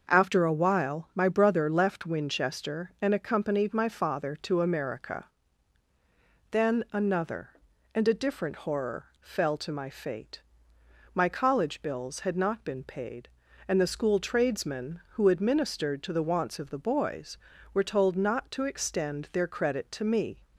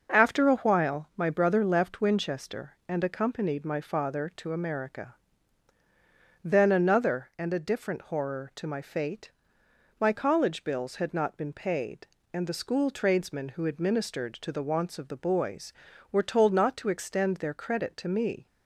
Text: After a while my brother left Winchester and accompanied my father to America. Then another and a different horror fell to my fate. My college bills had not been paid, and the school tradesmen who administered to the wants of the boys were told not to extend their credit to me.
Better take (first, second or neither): first